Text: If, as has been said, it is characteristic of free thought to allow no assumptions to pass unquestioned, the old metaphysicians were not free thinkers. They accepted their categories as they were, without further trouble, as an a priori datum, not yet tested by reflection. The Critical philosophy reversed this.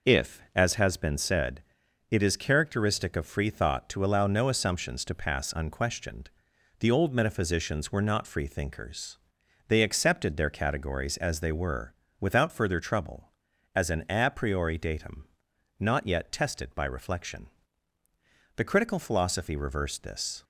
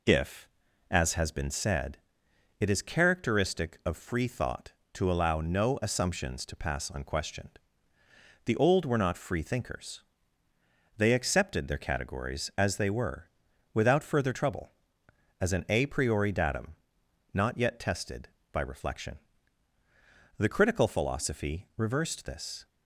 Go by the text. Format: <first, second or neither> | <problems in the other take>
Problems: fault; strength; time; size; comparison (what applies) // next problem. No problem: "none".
first | skips "metaphysicians"; at 8.8 s